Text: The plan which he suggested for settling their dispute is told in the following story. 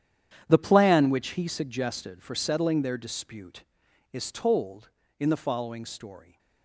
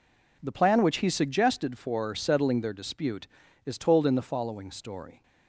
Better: second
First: gets quieter; strong; throughout; 15 dB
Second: none

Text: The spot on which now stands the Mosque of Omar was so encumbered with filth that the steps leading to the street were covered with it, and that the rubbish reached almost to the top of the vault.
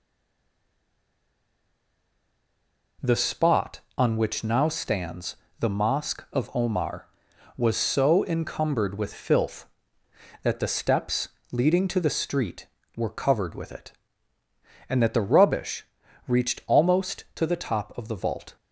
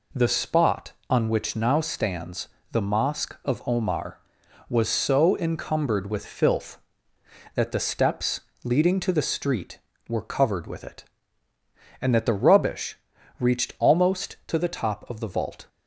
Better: second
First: stays silent before the first word; strong; until 2.9 s; 2.9 s long // pauses between "stands" and "the"; slight; at 5.3 s; 0.24 s long // pauses between "steps" and "leading"; slight; at 11.2 s; 0.20 s long // pauses between "rubbish" and "reached"; at 15.8 s; 0.42 s long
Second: pauses between "stands" and "the"; slight; at 2.4 s; 0.24 s long // pauses between "steps" and "leading"; slight; at 8.4 s; 0.20 s long // pauses between "rubbish" and "reached"; at 12.9 s; 0.42 s long

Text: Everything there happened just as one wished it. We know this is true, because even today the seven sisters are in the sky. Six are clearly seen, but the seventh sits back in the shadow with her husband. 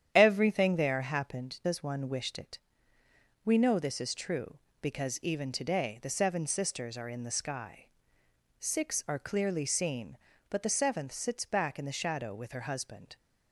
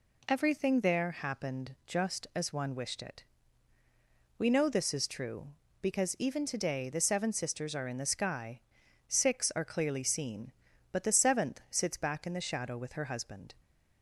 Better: second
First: starts louder than the rest; strong; until 1.1 s; 9.5 dB // skips "just"; at 1.6 s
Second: none

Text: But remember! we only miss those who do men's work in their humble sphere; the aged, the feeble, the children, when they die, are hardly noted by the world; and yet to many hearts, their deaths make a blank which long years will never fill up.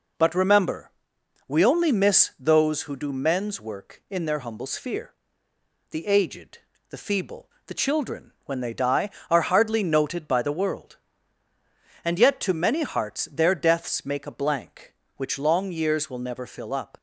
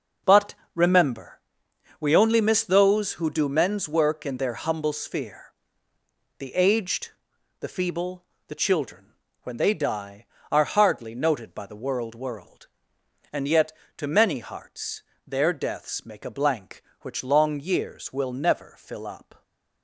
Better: first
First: none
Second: pauses between "But" and "remember"; slight; at 0.5 s; 0.18 s long // says "world" twice; at 12.1 s

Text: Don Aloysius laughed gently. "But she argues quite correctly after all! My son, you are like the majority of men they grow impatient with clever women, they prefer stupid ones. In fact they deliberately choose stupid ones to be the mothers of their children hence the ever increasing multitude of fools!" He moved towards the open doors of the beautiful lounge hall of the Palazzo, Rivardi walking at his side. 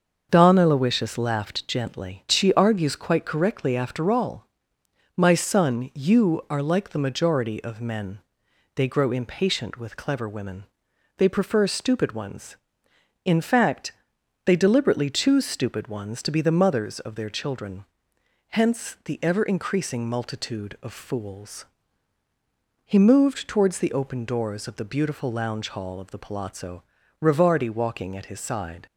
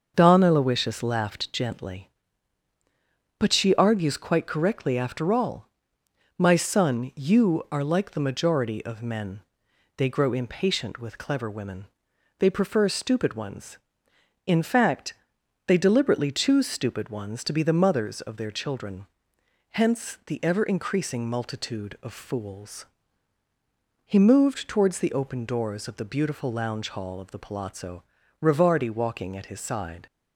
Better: second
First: starts louder than the rest; until 1.3 s; 6.5 dB // skips "But"; at 2.2 s // pauses between "men" and "they"; noticeable; at 8.1 s; 0.56 s long // pauses between "fact" and "they"; noticeable; at 13.9 s; 0.54 s long // pauses between "children" and "hence"; noticeable; at 17.8 s; 0.66 s long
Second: starts louder than the rest; until 1.1 s; 6.5 dB // pauses between "men" and "they"; noticeable; at 9.4 s; 0.56 s long // pauses between "fact" and "they"; noticeable; at 15.1 s; 0.54 s long // pauses between "children" and "hence"; noticeable; at 19.0 s; 0.66 s long

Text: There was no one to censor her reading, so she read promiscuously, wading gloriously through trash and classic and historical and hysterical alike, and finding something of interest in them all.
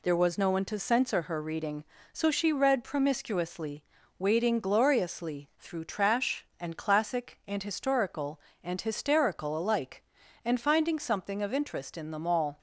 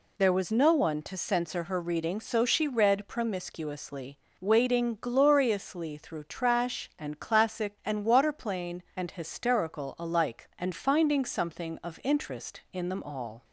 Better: first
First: none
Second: says "waterplane" for "historical"; at 8.0 s

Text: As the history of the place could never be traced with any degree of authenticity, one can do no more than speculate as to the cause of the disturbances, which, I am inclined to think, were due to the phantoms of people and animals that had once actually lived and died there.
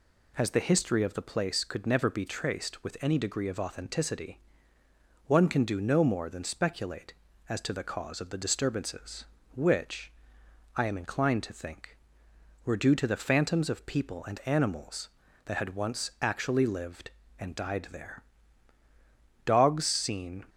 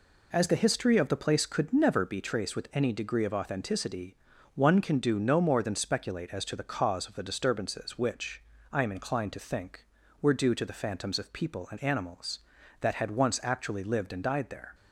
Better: second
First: goes on to say "Dogs seen"; noticeable; from 19.4 s on; 1.0 s long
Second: none

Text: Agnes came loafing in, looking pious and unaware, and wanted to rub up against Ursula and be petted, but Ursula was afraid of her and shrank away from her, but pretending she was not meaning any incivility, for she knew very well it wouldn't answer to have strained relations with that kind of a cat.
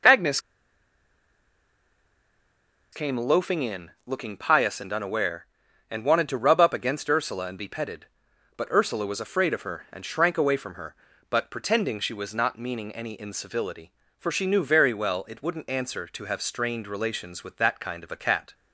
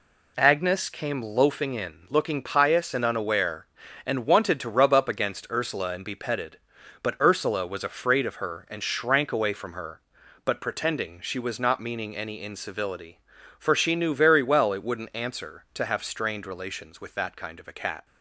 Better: second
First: pauses between "Agnes" and "came"; strong; at 0.3 s; 2.5 s long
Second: none

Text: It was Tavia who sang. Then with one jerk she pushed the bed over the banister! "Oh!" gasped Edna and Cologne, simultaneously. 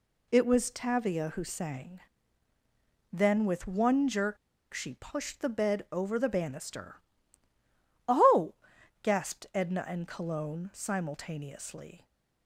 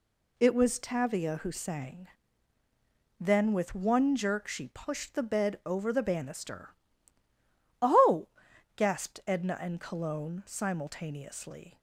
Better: second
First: pauses between "jerk" and "she"; at 4.3 s; 0.36 s long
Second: none

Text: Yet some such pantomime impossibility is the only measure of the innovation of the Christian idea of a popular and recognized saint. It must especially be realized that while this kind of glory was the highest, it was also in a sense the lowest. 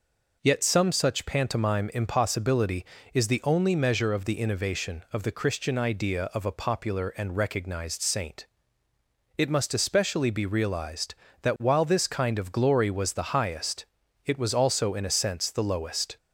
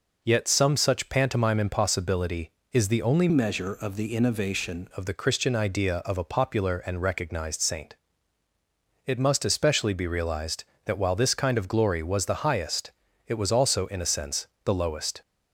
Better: first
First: none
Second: changes voice from "measure" to "innovation"; from 3.2 to 4.8 s; 1.6 s long // pauses between "sense" and "the"; slight; at 14.4 s; 0.18 s long

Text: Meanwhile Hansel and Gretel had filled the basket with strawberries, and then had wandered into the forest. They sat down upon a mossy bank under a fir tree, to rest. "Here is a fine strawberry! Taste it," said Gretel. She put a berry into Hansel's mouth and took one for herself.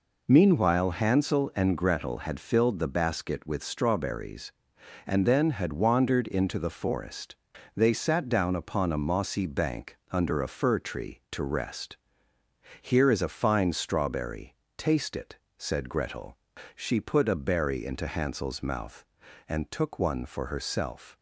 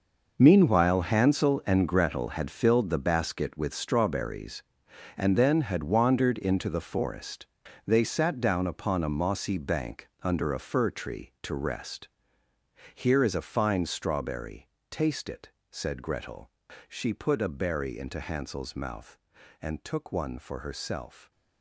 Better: first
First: none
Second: gets quieter; strong; throughout; 13 dB // stays silent after the last word; slight; from 21.0 s on; 0.6 s long

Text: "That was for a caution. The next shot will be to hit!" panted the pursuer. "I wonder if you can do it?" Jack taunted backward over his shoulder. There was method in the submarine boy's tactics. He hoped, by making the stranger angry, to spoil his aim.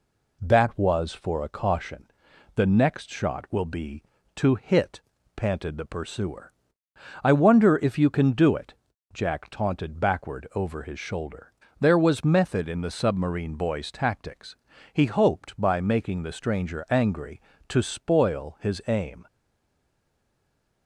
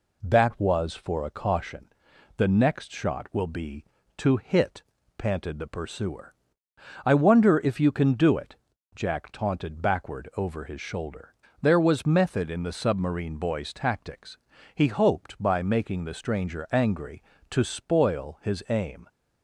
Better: second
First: stays silent after the last word; noticeable; from 19.2 s on; 1.6 s long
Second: none

